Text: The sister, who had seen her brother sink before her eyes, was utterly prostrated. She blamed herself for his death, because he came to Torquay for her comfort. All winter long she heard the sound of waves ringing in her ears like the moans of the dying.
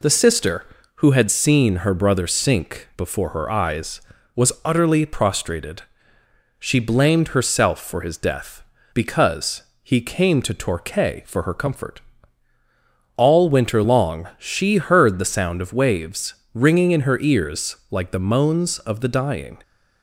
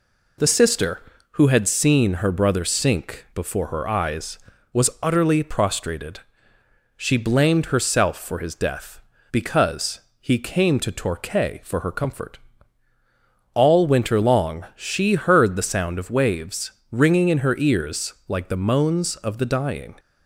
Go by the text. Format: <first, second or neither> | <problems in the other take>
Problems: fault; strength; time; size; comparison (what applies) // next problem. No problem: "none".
neither | pauses between "because" and "he"; slight; the same in both // pauses between "waves" and "ringing"; slight; the same in both